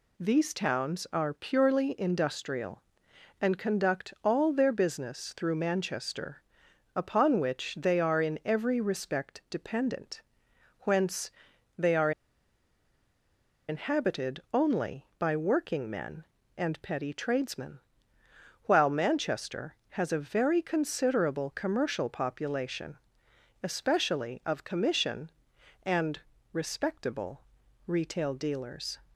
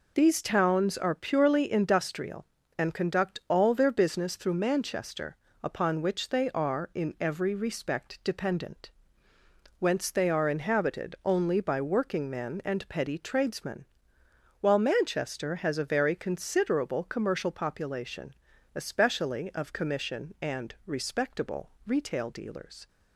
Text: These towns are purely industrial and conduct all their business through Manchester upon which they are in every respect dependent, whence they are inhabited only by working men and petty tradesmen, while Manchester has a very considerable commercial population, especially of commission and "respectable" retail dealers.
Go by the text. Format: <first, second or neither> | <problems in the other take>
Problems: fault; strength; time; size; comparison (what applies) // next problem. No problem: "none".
second | pauses between "Manchester" and "upon"; noticeable; at 6.4 s; 0.52 s long; slight in the second // pauses between "whence" and "they"; noticeable; at 11.3 s; 0.48 s long // pauses between "are" and "inhabited"; strong; at 12.1 s; 1.5 s long // pauses between "and" and "respectable"; slight; at 26.1 s; 0.34 s long // pauses between "respectable" and "retail"; at 27.4 s; 0.44 s long; slight in the second